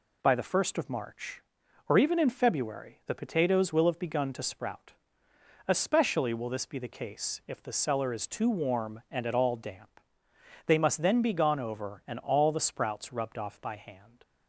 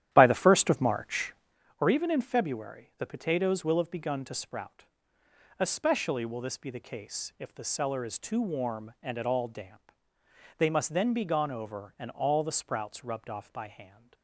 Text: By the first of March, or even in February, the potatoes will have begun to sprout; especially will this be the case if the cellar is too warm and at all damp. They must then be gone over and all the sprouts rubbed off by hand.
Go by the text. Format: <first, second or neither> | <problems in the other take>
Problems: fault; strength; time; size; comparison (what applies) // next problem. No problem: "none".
first | starts louder than the rest; strong; until 1.6 s; 11.5 dB